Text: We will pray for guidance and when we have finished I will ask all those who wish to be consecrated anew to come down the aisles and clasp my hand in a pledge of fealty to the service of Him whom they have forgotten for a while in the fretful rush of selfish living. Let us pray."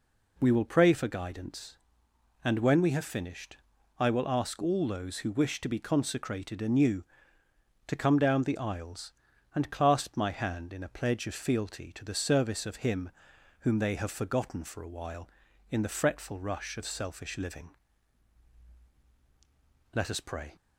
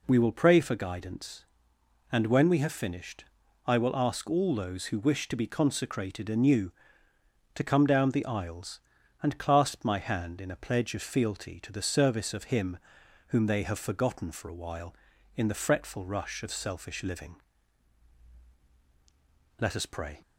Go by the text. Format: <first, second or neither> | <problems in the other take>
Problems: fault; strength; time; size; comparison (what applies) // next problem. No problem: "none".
neither | pauses between "finished" and "I"; the same in both // pauses between "Him" and "whom"; noticeable; the same in both